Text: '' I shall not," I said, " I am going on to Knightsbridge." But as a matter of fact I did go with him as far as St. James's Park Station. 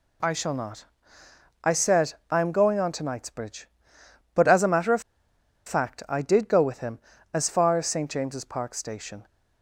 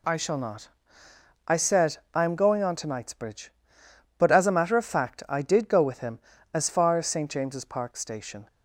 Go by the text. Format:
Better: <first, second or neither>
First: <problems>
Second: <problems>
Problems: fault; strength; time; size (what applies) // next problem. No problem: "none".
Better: second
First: pauses between "of" and "fact"; noticeable; at 5.0 s; 0.65 s long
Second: none